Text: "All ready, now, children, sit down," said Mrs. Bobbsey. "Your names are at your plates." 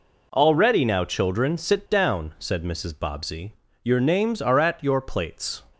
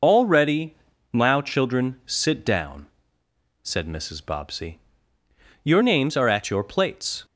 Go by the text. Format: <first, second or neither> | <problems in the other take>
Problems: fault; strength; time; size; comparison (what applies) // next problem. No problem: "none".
first | loses the start of "All"; at 0.0 s; 65 ms